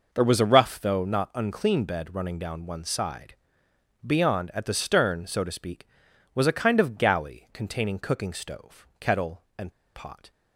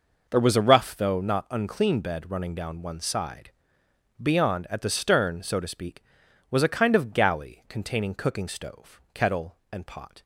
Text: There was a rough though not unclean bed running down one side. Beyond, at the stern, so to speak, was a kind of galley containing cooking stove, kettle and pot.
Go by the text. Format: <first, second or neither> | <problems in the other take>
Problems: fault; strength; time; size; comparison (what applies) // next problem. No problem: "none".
second | pauses between "and" and "pot"; slight; at 9.7 s; 0.23 s long